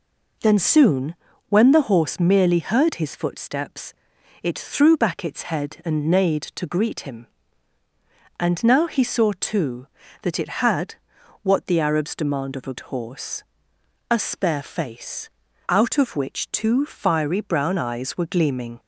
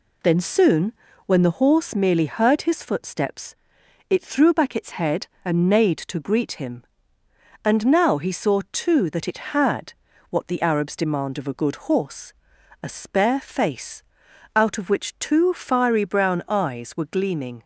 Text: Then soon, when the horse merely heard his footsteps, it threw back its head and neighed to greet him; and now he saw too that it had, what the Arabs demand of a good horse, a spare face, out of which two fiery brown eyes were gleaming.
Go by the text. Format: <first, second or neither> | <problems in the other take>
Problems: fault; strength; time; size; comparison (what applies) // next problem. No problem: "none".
second | skips "good"; at 12.8 s